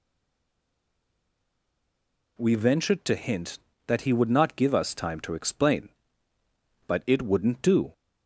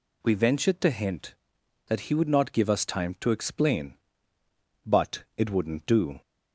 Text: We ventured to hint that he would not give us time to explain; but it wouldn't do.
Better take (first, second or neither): second